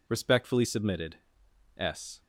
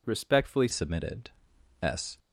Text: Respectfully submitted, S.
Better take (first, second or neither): first